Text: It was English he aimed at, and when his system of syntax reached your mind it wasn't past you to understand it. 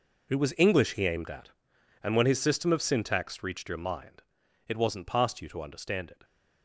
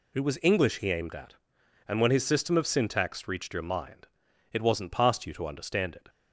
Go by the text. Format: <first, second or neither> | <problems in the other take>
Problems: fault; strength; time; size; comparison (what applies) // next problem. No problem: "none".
second | gets quieter; strong; throughout; 14.5 dB // pauses between "mind" and "it"; at 4.2 s; 0.44 s long; also in the second